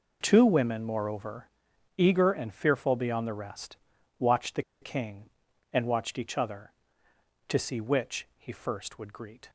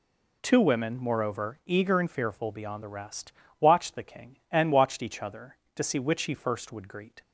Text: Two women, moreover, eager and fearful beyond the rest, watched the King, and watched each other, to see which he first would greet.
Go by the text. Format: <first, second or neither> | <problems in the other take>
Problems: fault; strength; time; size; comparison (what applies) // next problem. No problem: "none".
second | pauses between "the" and "King"; slight; at 4.6 s; 0.19 s long